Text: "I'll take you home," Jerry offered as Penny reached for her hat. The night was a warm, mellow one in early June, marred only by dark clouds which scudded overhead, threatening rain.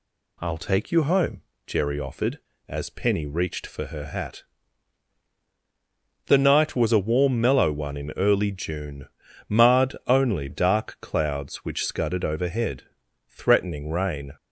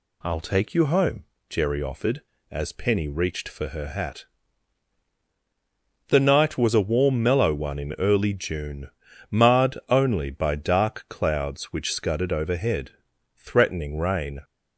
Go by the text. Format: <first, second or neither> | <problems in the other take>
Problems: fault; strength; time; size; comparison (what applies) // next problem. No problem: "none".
second | skips "by"; at 10.4 s